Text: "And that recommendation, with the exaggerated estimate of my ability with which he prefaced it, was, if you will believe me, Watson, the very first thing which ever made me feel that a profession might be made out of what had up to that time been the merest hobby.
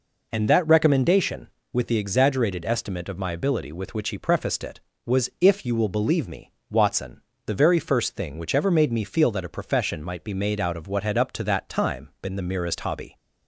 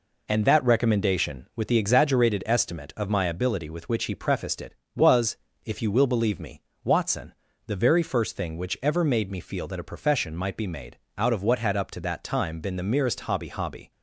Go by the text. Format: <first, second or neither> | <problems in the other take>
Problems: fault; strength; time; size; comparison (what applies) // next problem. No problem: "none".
first | pauses between "made" and "out"; slight; at 10.9 s; 0.20 s long // says "hobby" twice; at 13.4 s